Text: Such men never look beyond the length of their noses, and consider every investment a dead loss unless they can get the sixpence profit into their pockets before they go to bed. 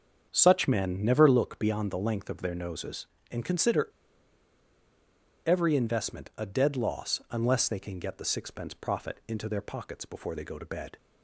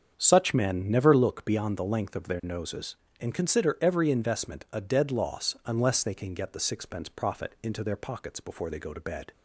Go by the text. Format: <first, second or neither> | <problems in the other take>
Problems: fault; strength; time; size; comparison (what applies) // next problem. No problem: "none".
second | starts louder than the rest; strong; until 1.3 s; 7 dB; strong in the second // pauses between "consider" and "every"; strong; at 3.8 s; 1.5 s long